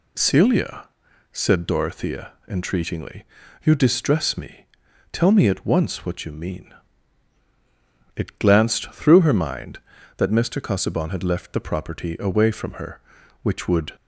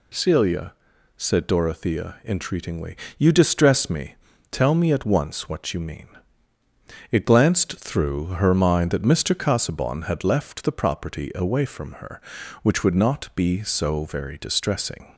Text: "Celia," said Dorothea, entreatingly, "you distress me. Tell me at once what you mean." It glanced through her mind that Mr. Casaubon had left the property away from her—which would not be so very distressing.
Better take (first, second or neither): second